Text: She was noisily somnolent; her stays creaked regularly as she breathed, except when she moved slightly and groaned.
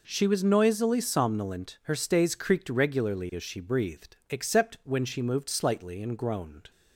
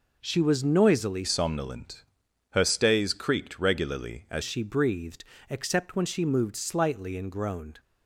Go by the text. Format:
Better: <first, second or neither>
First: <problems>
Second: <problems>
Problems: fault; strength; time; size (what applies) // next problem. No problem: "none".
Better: first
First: none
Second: changes voice from "somnolent" to "as"; from 1.2 to 4.4 s; 3.2 s long